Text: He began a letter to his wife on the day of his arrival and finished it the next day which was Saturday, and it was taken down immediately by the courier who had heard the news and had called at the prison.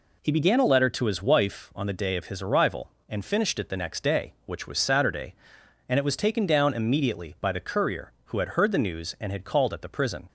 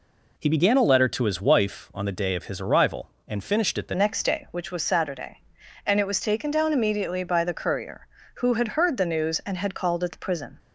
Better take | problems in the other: first | changes voice at "next"; from 3.9 s on; 6.6 s long

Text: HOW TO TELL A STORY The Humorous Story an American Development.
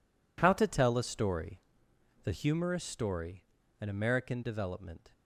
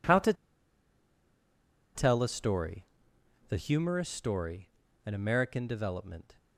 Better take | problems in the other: first | pauses between "TO" and "TELL"; strong; at 0.3 s; 1.6 s long // pauses between "STORY" and "The"; noticeable; at 2.8 s; 0.64 s long; noticeable in the first // pauses between "Story" and "an"; at 4.6 s; 0.38 s long; also in the first

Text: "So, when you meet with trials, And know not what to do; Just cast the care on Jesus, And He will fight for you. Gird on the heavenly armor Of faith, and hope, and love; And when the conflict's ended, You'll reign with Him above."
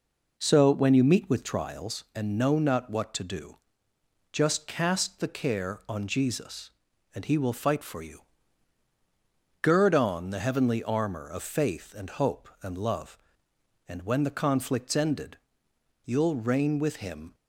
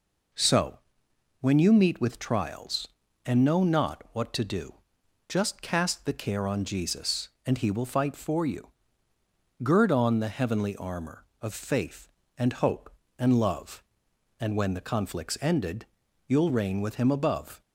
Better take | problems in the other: second | stops before "above"; at 17.3 s

